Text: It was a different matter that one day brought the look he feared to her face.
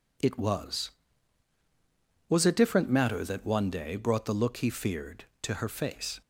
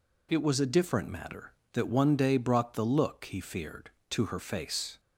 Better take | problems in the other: second | says "was" twice; at 2.2 s

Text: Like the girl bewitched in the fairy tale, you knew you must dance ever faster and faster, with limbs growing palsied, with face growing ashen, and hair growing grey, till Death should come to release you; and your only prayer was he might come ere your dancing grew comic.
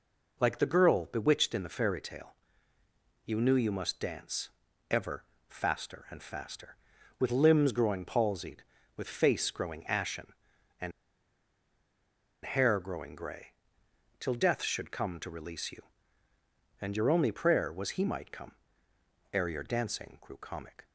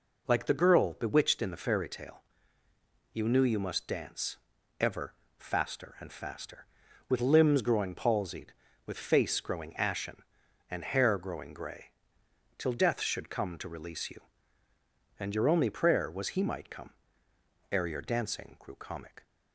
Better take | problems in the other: second | pauses between "dance" and "ever"; at 4.4 s; 0.38 s long; also in the second // pauses between "ever" and "faster"; slight; at 5.2 s; 0.24 s long; slight in the second // pauses between "and" and "hair"; strong; at 10.9 s; 1.5 s long // pauses between "come" and "ere"; noticeable; at 18.5 s; 0.82 s long; noticeable in the second

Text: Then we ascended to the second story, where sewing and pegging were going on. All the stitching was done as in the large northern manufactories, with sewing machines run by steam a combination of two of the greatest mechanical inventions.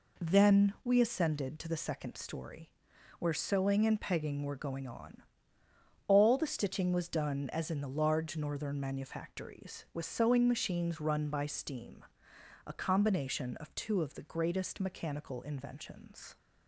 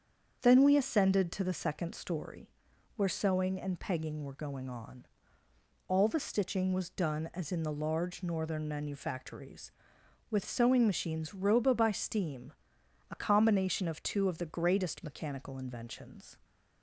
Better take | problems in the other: first | starts louder than the rest; strong; until 1.4 s; 7.5 dB // says "roba" for "run"; at 11.3 s // pauses between "steam" and "a"; noticeable; at 12.5 s; 0.58 s long; noticeable in the first

